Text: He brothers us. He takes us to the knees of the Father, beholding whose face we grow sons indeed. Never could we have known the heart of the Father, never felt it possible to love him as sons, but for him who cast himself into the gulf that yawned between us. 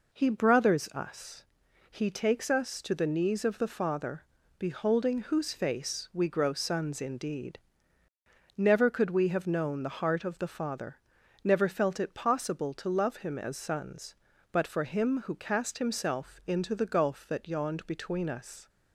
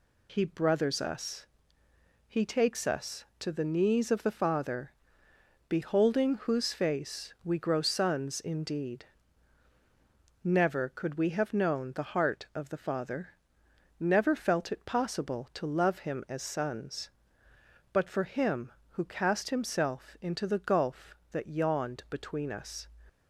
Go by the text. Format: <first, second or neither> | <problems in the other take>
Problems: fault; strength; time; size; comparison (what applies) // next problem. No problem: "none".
neither | none